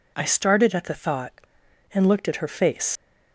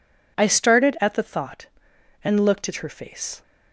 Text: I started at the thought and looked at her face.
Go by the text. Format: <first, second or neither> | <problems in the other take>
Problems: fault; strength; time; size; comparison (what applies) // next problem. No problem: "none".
second | leaves "face" unfinished; at 2.9 s; 85 ms